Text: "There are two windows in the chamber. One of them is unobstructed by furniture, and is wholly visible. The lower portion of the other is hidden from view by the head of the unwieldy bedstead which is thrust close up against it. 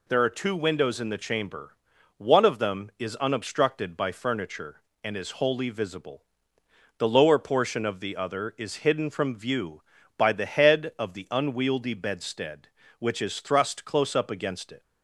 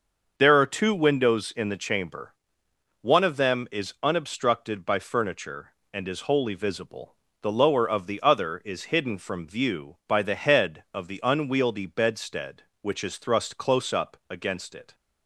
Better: first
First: none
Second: starts louder than the rest; until 1.4 s; 6 dB // skips "portion"; at 7.8 s

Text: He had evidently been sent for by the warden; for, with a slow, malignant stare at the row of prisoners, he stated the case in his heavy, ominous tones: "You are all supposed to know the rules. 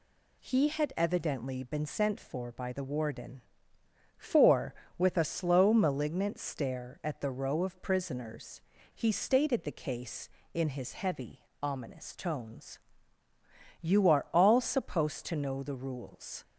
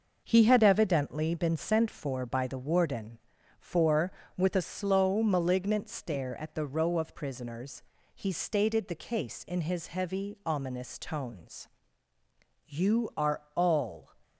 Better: first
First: none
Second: pauses between "are" and "all"; slight; at 13.3 s; 0.16 s long // stops before "supposed to know the rules"; at 14.2 s

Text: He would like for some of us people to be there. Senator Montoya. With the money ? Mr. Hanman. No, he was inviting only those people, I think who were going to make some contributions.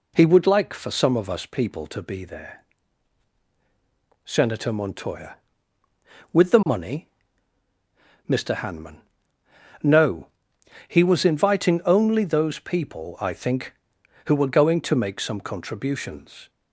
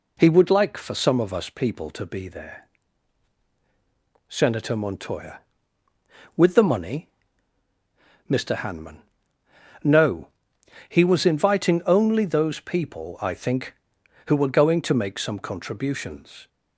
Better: neither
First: none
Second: none

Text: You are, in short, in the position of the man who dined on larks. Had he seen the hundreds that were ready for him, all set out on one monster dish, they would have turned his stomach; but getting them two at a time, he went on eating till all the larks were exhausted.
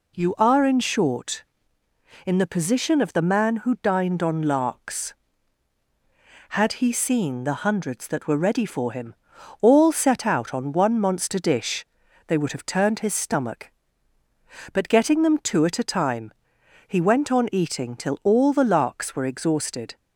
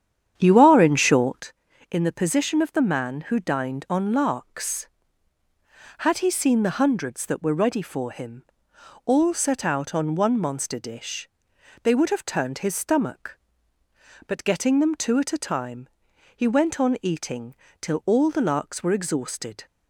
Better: first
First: none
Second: starts louder than the rest; strong; until 1.5 s; 9 dB // pauses between "eating" and "till"; slight; at 17.5 s; 0.24 s long

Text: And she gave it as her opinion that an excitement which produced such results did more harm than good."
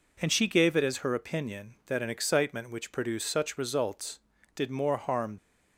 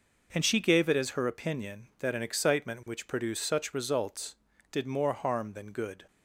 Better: second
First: stops before "than good"; at 5.3 s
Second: none

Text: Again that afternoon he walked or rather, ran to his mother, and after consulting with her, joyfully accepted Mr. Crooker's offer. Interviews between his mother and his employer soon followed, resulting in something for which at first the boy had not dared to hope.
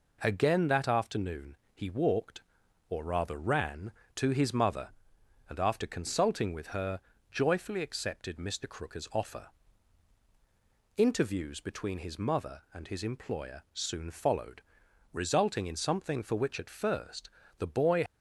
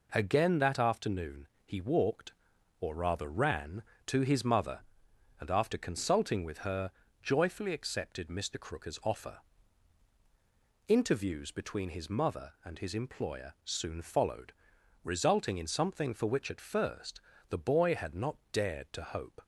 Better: second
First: pauses between "afternoon" and "he"; slight; at 1.5 s; 0.18 s long // pauses between "first" and "the"; slight; at 17.2 s; 0.30 s long // stops before "had not dared to hope"; at 18.0 s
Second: pauses between "afternoon" and "he"; slight; at 1.4 s; 0.18 s long // pauses between "first" and "the"; slight; at 17.2 s; 0.30 s long

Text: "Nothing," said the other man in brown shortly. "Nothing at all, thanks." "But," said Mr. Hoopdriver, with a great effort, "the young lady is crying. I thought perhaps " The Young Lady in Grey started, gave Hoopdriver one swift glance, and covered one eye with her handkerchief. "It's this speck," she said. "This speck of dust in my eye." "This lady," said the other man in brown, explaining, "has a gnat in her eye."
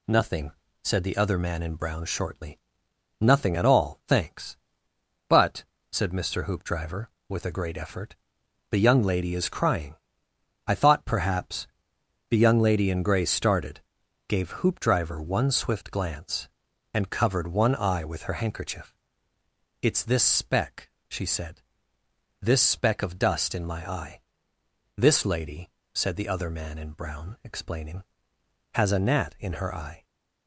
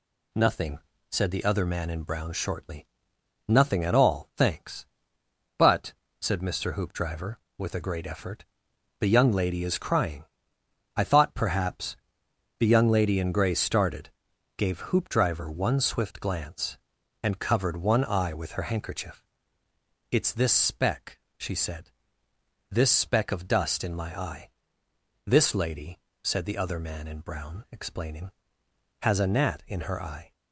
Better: neither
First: none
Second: none

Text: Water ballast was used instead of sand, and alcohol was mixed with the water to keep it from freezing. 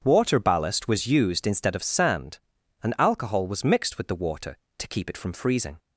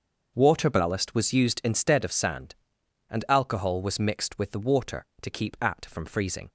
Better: first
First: starts louder than the rest; strong; until 1.0 s; 7.5 dB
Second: starts louder than the rest; until 1.3 s; 6.5 dB // says "at" for "it"; at 5.6 s

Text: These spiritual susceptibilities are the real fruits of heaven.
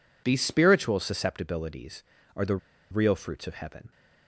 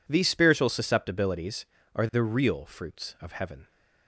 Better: second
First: pauses between "the" and "real"; slight; at 2.5 s; 0.33 s long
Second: none

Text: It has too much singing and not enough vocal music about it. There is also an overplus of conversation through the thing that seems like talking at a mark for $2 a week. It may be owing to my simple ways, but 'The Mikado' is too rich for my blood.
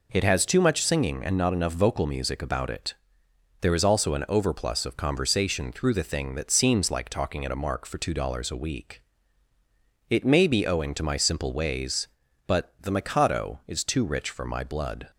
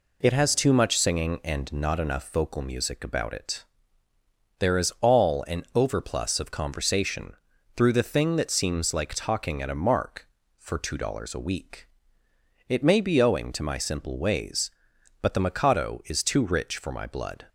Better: first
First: none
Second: says "all" for "also"; at 5.0 s // pauses between "conversation" and "through"; at 7.3 s; 0.42 s long

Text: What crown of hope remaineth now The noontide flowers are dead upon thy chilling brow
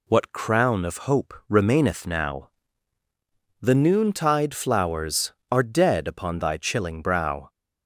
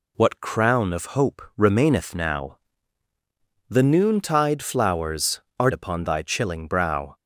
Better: first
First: pauses between "hope" and "remaineth"; slight; at 1.3 s; 0.16 s long // pauses between "now" and "The"; at 2.4 s; 1.1 s long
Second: pauses between "hope" and "remaineth"; slight; at 1.4 s; 0.16 s long // pauses between "now" and "The"; at 2.5 s; 1.1 s long // skips "dead"; at 5.7 s

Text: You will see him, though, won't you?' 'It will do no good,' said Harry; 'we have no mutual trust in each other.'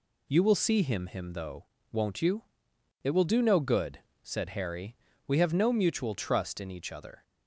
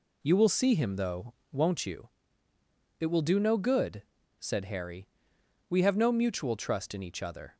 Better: second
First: says "him" twice; at 1.0 s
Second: none

